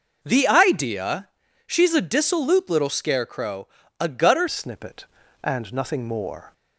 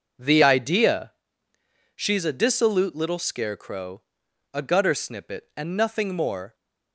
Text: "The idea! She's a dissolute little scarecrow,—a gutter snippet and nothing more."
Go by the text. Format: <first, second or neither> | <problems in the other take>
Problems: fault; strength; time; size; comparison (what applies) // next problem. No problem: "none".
second | changes voice at "snippet"; from 4.4 s on; 2.1 s long